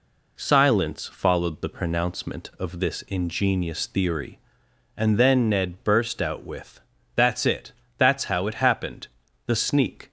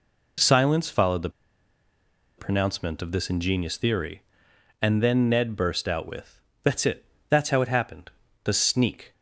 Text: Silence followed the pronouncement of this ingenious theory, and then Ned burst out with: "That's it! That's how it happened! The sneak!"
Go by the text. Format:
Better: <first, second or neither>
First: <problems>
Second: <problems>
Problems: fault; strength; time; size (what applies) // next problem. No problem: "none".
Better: first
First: none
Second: pauses between "the" and "pronouncement"; at 1.2 s; 1.0 s long